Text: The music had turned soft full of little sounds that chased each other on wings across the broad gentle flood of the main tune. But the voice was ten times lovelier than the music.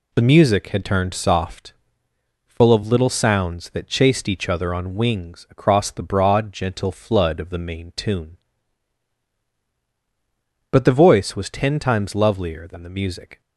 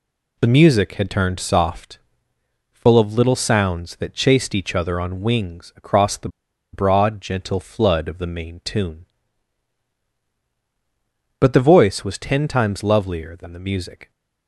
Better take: first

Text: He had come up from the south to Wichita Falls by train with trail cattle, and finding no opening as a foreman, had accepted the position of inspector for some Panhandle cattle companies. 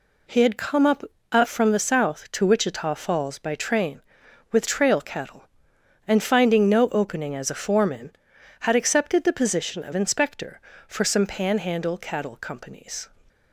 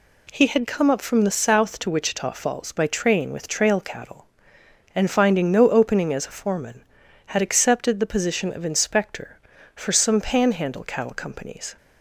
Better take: second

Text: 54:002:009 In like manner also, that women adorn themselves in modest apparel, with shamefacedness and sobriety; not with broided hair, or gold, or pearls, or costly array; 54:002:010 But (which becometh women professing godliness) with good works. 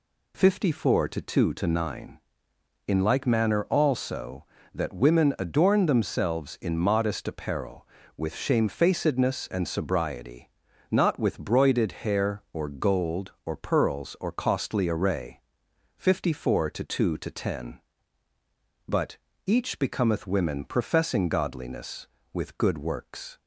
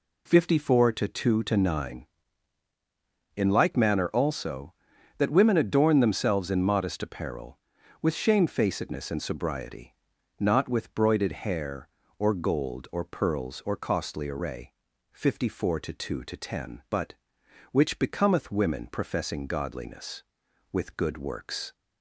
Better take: second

